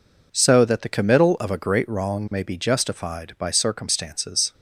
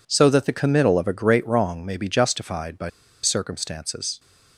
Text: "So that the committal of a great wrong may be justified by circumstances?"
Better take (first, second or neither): first